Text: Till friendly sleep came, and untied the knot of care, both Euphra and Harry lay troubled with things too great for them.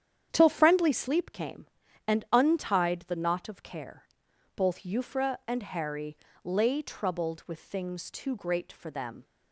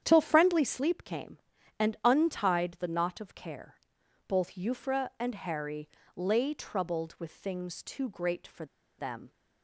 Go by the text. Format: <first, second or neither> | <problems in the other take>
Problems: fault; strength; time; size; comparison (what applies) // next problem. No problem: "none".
first | starts louder than the rest; strong; until 1.0 s; 9 dB; strong in the first // pauses between "Harry" and "lay"; slight; at 5.8 s; 0.26 s long; slight in the first // pauses between "for" and "them"; slight; at 8.6 s; 0.33 s long